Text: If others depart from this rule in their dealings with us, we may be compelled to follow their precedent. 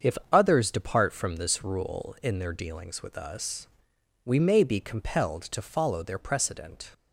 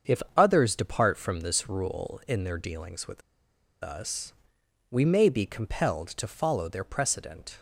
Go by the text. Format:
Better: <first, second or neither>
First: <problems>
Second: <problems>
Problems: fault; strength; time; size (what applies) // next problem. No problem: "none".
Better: first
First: starts louder than the rest; until 1.1 s; 7 dB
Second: starts louder than the rest; until 1.2 s; 7 dB // pauses between "with" and "us"; noticeable; at 3.2 s; 0.63 s long